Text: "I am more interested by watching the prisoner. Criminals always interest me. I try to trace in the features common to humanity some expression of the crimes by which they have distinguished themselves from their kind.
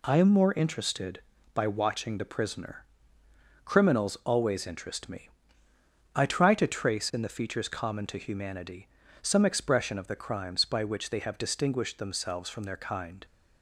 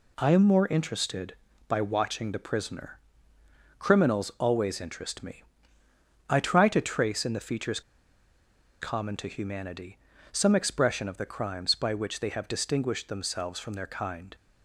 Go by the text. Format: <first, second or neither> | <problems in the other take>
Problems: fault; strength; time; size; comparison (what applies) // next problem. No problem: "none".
first | pauses between "features" and "common"; at 7.8 s; 1.0 s long // pauses between "humanity" and "some"; slight; at 9.9 s; 0.32 s long; slight in the first